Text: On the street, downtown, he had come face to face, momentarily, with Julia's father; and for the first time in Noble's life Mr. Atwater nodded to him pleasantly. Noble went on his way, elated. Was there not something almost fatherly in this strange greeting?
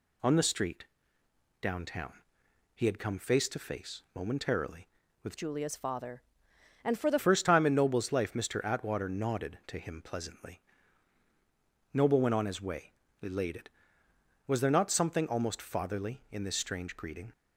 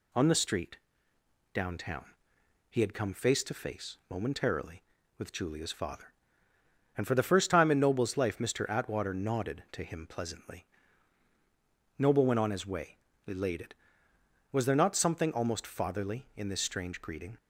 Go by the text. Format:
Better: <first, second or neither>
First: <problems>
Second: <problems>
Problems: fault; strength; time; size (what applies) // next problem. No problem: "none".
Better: second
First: changes voice from "Julia's" to "the"; from 5.3 to 7.1 s; 1.8 s long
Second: none